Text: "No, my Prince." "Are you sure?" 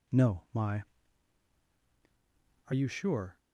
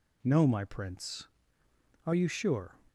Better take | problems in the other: second | skips "Prince"; at 1.7 s

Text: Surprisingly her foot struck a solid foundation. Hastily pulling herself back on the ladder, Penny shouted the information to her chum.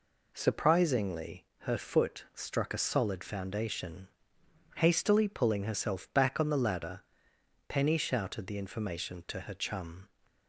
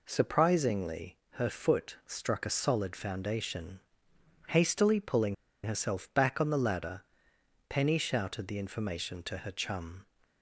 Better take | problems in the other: first | pauses between "pulling" and "herself"; slight; at 5.3 s; 0.29 s long

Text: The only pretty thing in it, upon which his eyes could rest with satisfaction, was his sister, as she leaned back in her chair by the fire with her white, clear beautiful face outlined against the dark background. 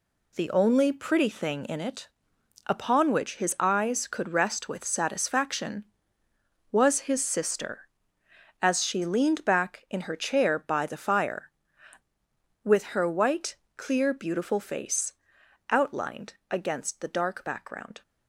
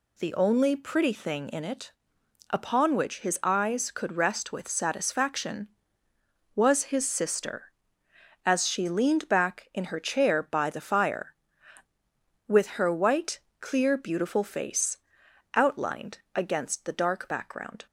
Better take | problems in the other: second | gets quieter; strong; throughout; 8 dB // pauses between "face" and "outlined"; noticeable; at 15.1 s; 0.56 s long; noticeable in the second // pauses between "outlined" and "against"; slight; at 16.3 s; 0.16 s long; slight in the second

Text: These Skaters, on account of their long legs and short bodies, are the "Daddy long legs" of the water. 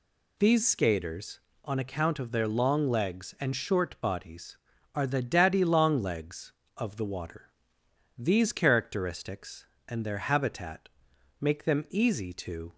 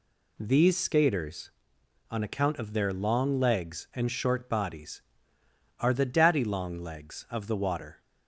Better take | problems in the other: second | goes on to say "These characteristics and their habitat make them easy to"; strong; from 8.1 s on; 4.5 s long

